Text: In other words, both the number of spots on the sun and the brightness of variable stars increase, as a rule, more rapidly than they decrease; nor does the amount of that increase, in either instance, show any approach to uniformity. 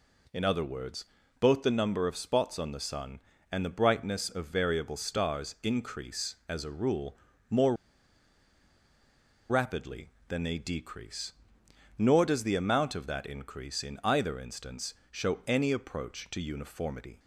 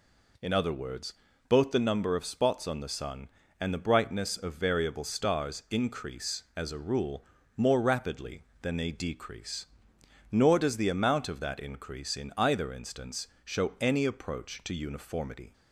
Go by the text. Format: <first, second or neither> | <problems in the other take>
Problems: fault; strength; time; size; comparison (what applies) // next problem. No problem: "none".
second | pauses between "more" and "rapidly"; strong; at 7.7 s; 1.7 s long